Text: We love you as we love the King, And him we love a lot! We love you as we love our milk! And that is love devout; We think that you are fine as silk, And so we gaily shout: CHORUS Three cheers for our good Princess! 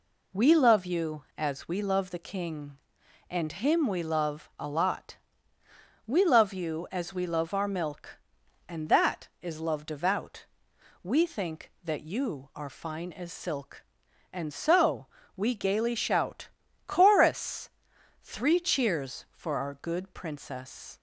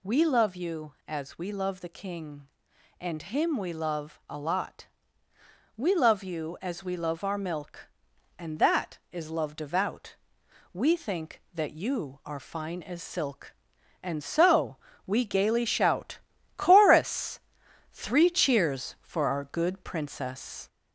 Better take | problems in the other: first | gets louder; slight; throughout; 3.5 dB // pauses between "so" and "we"; slight; at 14.7 s; 0.32 s long; slight in the first // pauses between "CHORUS" and "Three"; noticeable; at 17.3 s; 0.54 s long; noticeable in the first

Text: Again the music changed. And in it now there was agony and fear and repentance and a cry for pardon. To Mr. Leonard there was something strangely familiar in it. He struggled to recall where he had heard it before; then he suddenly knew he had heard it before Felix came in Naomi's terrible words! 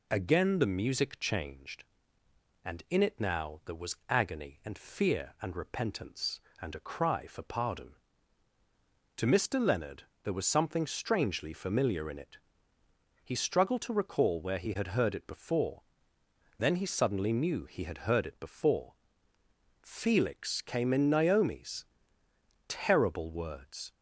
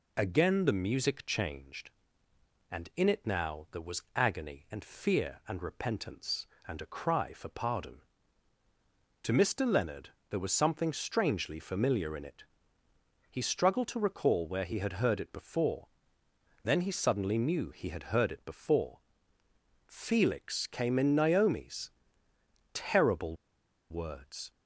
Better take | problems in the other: first | pauses between "Leonard" and "there"; slight; at 10.1 s; 0.20 s long; slight in the first // pauses between "before" and "Felix"; noticeable; at 18.9 s; 0.88 s long; noticeable in the first // pauses between "Naomi's" and "terrible"; noticeable; at 21.9 s; 0.84 s long; noticeable in the first // pauses between "terrible" and "words"; noticeable; at 23.3 s; 0.56 s long

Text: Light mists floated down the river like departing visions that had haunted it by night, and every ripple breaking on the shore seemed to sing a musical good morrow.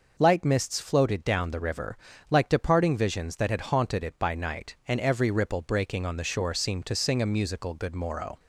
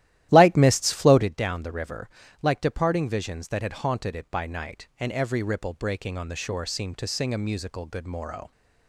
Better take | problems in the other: first | starts louder than the rest; strong; until 1.3 s; 14 dB // pauses between "river" and "like"; slight; at 2.0 s; 0.36 s long; slight in the first

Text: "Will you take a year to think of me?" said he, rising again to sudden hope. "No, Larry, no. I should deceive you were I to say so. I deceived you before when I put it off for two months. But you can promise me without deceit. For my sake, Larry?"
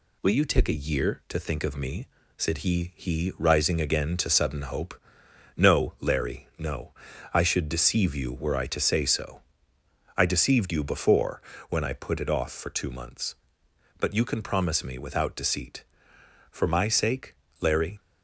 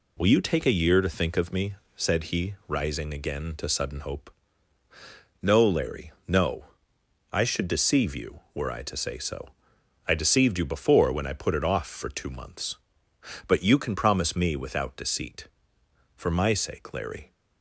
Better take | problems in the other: second | says "he" twice; at 2.9 s // pauses between "before" and "when"; slight; at 11.3 s; 0.30 s long

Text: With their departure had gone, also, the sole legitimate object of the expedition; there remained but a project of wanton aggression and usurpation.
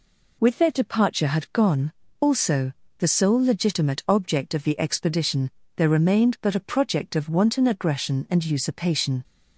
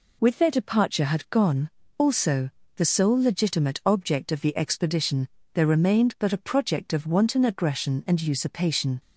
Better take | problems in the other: neither | none

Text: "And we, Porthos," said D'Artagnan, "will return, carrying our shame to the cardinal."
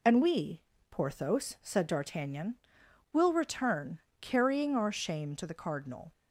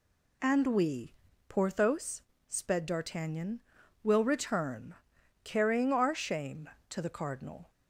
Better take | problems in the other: first | says "sped" for "said"; at 2.4 s

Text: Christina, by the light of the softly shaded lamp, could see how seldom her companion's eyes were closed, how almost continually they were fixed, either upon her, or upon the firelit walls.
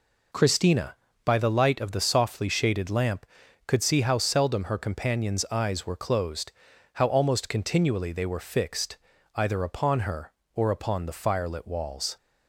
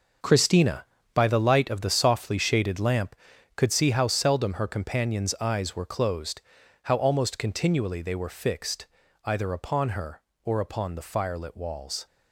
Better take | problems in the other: first | gets quieter; strong; throughout; 10.5 dB

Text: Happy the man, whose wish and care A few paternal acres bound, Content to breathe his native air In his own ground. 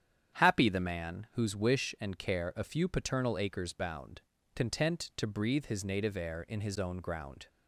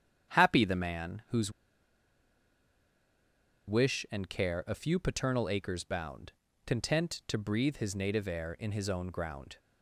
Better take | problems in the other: first | starts louder than the rest; strong; until 1.3 s; 9 dB; strong in the first // pauses between "whose" and "wish"; strong; at 1.5 s; 2.1 s long

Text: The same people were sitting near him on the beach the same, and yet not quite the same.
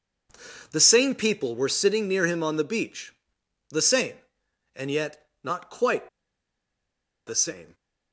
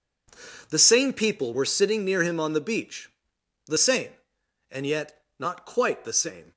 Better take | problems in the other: second | pauses between "beach" and "the"; noticeable; at 3.1 s; 0.56 s long; noticeable in the second // pauses between "yet" and "not"; slight; at 5.2 s; 0.16 s long; slight in the second // pauses between "quite" and "the"; at 6.0 s; 1.1 s long

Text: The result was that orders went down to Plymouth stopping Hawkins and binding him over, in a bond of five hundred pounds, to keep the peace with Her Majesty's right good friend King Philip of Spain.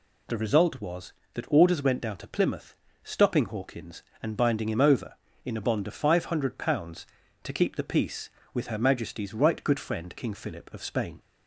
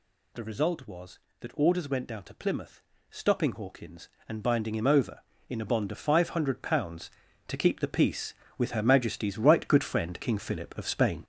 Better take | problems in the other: first | gets louder; throughout; 6.5 dB // pauses between "Plymouth" and "stopping"; slight; at 2.8 s; 0.30 s long; slight in the first

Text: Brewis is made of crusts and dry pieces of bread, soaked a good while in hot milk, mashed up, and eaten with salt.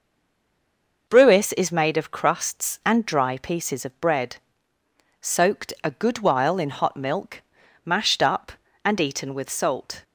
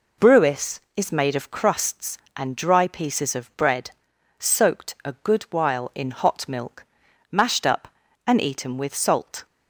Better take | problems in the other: second | stays silent before the first word; until 1.0 s; 1.0 s long

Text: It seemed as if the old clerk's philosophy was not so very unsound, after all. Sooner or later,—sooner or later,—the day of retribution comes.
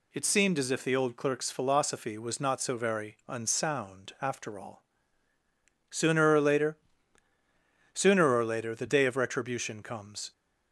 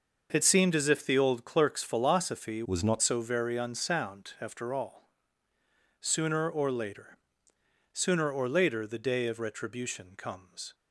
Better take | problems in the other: first | changes voice from "was" to "not"; from 2.6 to 3.0 s; 0.4 s long

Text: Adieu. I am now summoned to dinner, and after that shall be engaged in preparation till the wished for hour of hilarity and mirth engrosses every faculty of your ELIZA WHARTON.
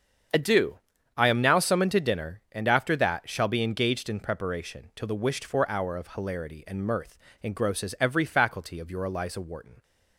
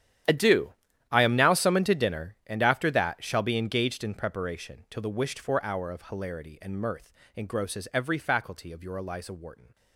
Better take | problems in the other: first | gets quieter; strong; throughout; 17.5 dB // starts louder than the rest; strong; until 1.6 s; 10.5 dB; strong in the first // pauses between "mirth" and "engrosses"; slight; at 7.1 s; 0.24 s long; slight in the first

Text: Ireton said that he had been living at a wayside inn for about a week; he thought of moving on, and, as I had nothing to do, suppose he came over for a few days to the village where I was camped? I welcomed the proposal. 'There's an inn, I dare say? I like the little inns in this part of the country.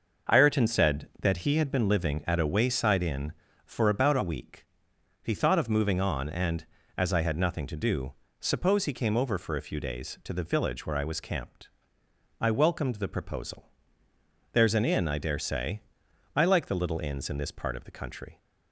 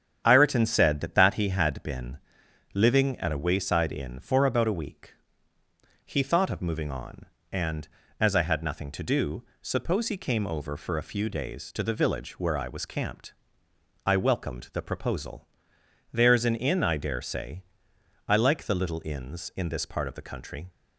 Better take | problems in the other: first | starts louder than the rest; strong; until 1.2 s; 8.5 dB // says "that" twice; at 1.1 s // pauses between "been" and "living"; noticeable; at 2.1 s; 0.56 s long

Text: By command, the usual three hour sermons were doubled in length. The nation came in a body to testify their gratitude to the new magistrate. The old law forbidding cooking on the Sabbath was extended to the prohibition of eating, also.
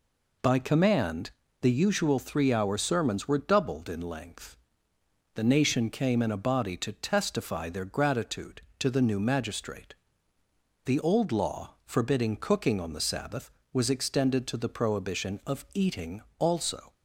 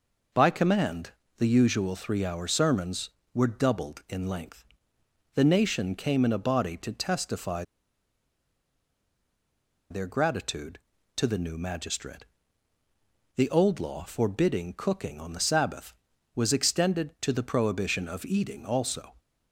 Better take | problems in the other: first | pauses between "testify" and "their"; strong; at 7.6 s; 2.2 s long

